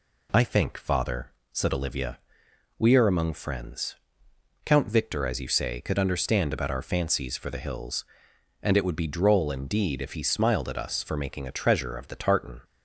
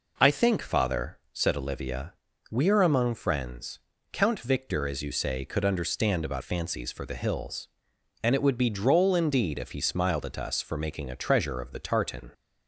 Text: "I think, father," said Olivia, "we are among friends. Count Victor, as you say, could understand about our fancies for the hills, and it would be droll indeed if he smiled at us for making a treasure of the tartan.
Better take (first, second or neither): first